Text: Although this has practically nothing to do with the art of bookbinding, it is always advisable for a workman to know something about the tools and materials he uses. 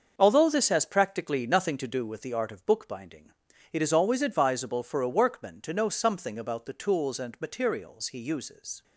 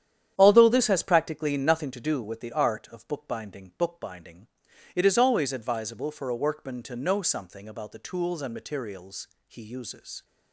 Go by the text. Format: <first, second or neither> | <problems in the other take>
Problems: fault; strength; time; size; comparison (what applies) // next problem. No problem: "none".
first | starts louder than the rest; strong; until 1.3 s; 9.5 dB; also in the first // says "bookbinding" twice; at 3.7 s // pauses between "materials" and "he"; slight; at 9.2 s; 0.18 s long